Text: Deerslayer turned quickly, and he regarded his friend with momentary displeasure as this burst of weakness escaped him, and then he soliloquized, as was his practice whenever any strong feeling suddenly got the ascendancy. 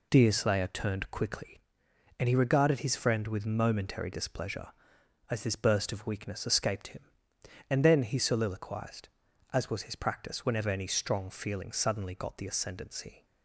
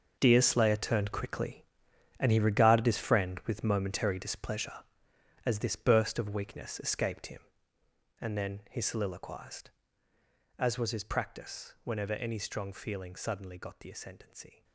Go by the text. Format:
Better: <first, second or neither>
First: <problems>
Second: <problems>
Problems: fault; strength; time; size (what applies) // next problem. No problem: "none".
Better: first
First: none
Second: gets quieter; strong; throughout; 13.5 dB